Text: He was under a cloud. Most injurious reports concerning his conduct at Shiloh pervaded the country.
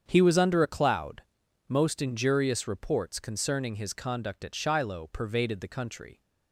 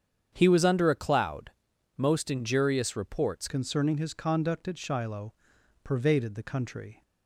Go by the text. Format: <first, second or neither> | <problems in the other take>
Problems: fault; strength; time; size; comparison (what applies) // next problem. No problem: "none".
first | starts louder than the rest; strong; until 1.3 s; 8 dB; strong in the first // changes voice at "concerning"; from 3.4 s on; 3.6 s long // pauses between "Shiloh" and "pervaded"; noticeable; at 5.3 s; 0.52 s long